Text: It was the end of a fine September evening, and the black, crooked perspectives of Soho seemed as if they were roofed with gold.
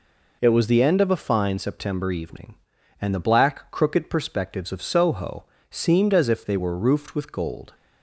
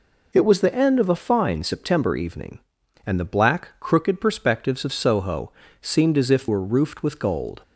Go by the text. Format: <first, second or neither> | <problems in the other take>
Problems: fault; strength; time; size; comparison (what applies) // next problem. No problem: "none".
first | pauses between "Soho" and "seemed"; slight; at 5.5 s; 0.30 s long; slight in the first // skips "they"; at 6.4 s